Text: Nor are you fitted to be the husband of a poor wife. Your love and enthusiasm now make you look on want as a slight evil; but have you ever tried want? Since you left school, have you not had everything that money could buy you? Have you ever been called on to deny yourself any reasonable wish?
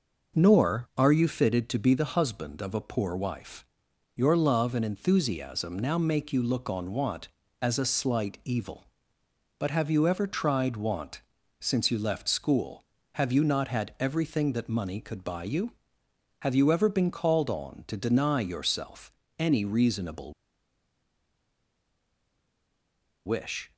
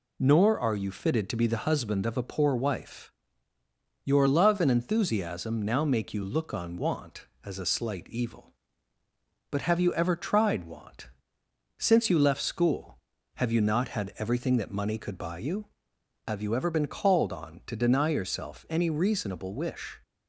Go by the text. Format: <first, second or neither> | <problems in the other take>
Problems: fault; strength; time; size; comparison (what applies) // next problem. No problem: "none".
second | pauses between "yourself" and "any"; slight; at 19.1 s; 0.26 s long // pauses between "reasonable" and "wish"; strong; at 20.3 s; 2.9 s long